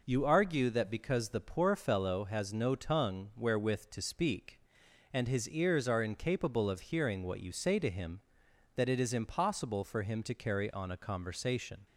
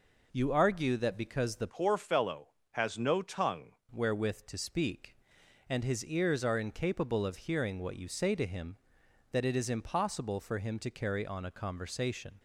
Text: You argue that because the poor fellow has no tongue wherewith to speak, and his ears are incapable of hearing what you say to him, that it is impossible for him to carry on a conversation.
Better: first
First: none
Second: changes voice from "poor" to "tongue"; from 1.6 to 3.7 s; 2.1 s long

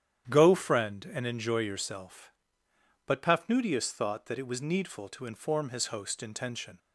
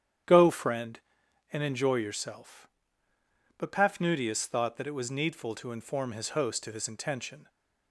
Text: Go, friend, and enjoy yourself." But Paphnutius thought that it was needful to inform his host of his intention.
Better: second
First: starts louder than the rest; strong; until 1.3 s; 10.5 dB // skips "of his"; at 6.2 s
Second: starts louder than the rest; strong; until 1.7 s; 10 dB

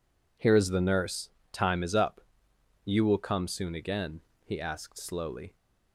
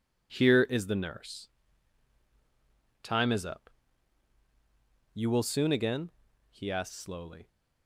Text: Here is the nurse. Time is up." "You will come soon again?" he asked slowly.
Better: first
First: none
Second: skips "come"; at 5.4 s

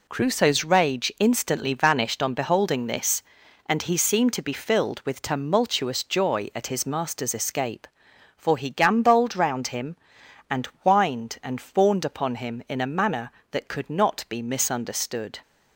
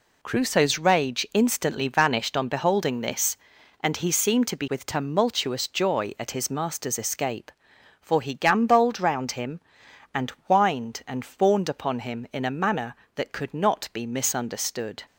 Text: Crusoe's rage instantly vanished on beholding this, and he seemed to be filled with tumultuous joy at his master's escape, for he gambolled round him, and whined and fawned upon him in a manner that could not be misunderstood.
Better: first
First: pauses between "and" and "whined"; slight; at 10.6 s; 0.18 s long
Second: skips "filled"; at 4.6 s // pauses between "and" and "whined"; slight; at 10.3 s; 0.18 s long

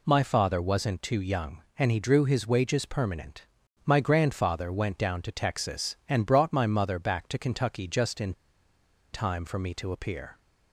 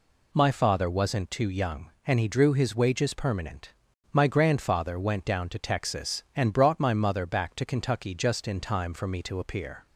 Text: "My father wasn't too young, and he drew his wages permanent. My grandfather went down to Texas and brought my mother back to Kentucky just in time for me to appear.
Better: second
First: pauses between "in" and "time"; noticeable; at 8.3 s; 0.81 s long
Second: none

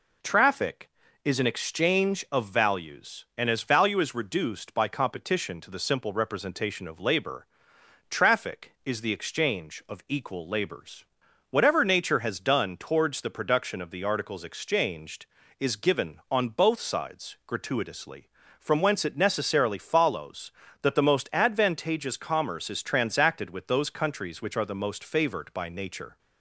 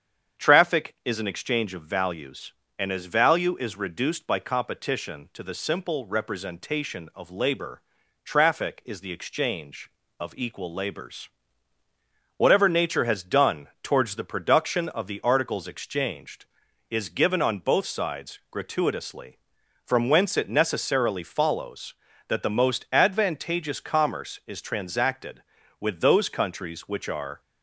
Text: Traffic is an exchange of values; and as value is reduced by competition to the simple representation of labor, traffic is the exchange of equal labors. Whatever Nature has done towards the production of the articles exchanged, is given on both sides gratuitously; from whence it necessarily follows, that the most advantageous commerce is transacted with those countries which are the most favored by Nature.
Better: first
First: none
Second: starts louder than the rest; strong; until 1.4 s; 8 dB // stops before "the most favored by Nature"; at 27.4 s

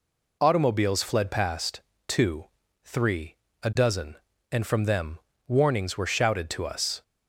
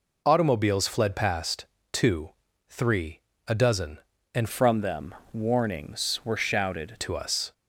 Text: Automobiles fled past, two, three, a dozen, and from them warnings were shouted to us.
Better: first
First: pauses between "them" and "warnings"; slight; at 5.1 s; 0.28 s long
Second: changes voice from "from" to "shouted"; from 4.5 to 6.9 s; 2.4 s long // pauses between "them" and "warnings"; slight; at 5.1 s; 0.20 s long

